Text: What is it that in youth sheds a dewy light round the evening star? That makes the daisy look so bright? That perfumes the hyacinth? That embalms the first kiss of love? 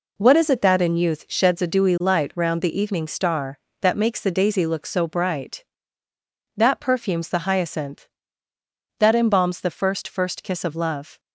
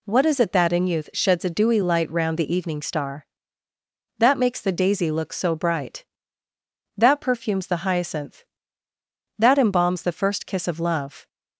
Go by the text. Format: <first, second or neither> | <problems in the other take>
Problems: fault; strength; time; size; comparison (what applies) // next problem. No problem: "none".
second | says "first" twice; at 10.0 s